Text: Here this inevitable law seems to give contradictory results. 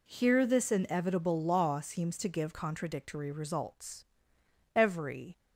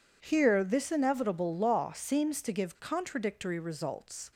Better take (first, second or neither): second